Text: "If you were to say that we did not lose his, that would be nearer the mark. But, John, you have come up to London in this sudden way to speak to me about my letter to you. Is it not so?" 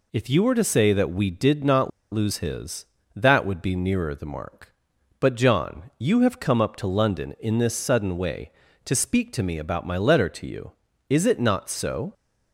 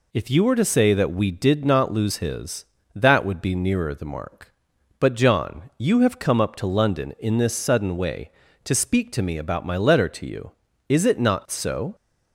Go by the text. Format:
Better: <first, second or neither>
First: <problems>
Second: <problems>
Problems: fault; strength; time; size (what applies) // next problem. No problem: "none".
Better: second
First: pauses between "not" and "lose"; slight; at 1.9 s; 0.22 s long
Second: none